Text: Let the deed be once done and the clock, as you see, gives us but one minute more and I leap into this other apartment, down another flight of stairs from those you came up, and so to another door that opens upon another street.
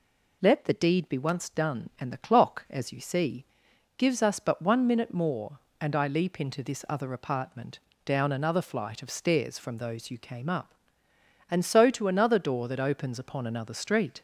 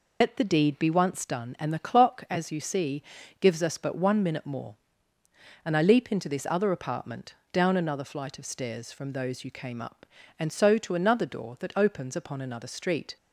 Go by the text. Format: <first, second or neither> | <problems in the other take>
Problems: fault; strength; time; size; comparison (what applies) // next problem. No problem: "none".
first | loses the start of "Let"; at 0.2 s; 85 ms